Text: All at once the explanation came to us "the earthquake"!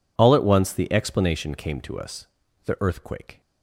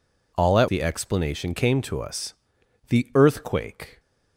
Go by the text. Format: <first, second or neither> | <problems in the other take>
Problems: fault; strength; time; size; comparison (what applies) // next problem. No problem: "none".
first | skips "once"; at 0.6 s // pauses between "us" and "the"; noticeable; at 2.3 s; 0.54 s long; also in the first